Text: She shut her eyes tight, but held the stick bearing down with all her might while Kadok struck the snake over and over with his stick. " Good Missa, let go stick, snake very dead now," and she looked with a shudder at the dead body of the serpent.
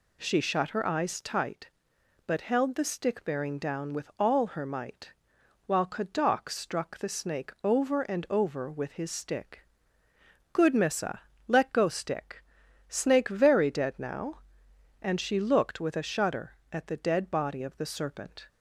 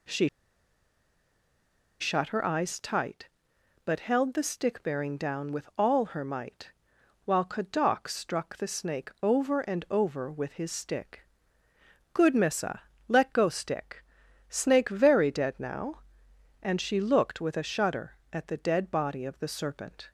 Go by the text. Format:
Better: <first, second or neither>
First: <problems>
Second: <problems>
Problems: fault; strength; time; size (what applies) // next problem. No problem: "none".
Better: first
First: pauses between "might" and "while"; noticeable; at 5.1 s; 0.54 s long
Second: pauses between "She" and "shut"; strong; at 0.2 s; 1.7 s long // pauses between "might" and "while"; noticeable; at 6.7 s; 0.54 s long